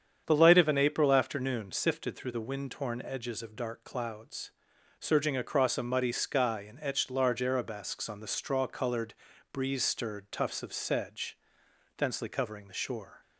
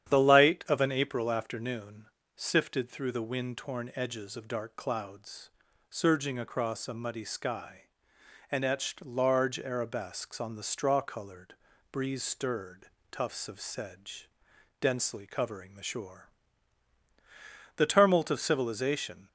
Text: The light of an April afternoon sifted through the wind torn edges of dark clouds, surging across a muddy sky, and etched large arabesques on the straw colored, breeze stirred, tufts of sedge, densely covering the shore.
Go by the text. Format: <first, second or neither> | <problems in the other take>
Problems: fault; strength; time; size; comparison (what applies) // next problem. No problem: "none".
first | starts louder than the rest; strong; until 1.1 s; 9.5 dB; strong in the first // pauses between "afternoon" and "sifted"; slight; at 2.0 s; 0.32 s long // goes on to say "The tumult of civilization"; from 17.7 s on; 1.5 s long